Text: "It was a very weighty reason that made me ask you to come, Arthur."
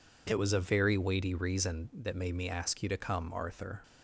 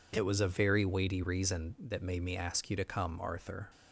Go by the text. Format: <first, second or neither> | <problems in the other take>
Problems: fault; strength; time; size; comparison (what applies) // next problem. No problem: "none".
neither | none